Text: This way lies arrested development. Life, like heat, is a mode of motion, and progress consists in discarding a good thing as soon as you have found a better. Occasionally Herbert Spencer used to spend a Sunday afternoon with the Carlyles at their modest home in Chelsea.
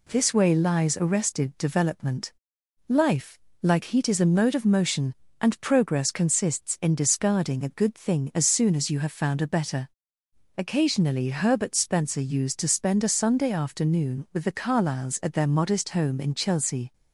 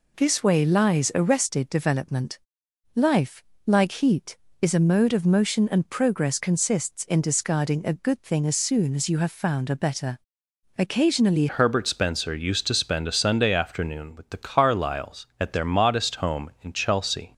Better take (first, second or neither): first